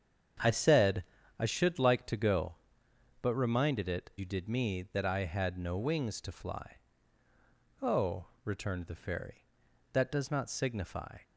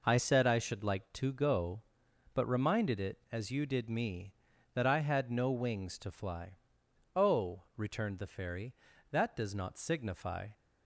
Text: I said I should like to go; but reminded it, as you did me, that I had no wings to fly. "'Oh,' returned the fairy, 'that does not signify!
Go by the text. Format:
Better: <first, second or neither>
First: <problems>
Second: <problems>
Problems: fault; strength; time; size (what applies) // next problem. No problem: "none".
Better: second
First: starts louder than the rest; strong; until 1.7 s; 7.5 dB // pauses between "said" and "I"; slight; at 1.0 s; 0.34 s long // skips "as"; at 4.1 s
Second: none